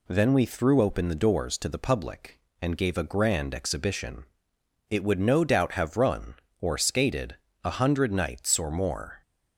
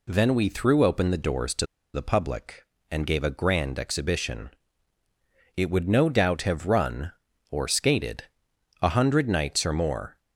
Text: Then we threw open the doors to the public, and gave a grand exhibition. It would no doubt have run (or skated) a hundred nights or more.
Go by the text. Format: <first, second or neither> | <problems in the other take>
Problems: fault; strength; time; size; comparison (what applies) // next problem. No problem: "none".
first | pauses between "to" and "the"; slight; at 1.6 s; 0.28 s long